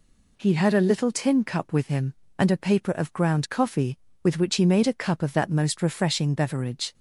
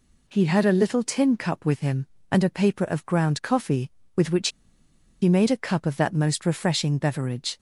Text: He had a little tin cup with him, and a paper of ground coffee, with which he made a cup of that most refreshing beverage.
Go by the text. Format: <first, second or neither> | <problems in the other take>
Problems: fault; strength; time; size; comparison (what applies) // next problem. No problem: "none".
first | pauses between "which" and "he"; noticeable; at 4.4 s; 0.72 s long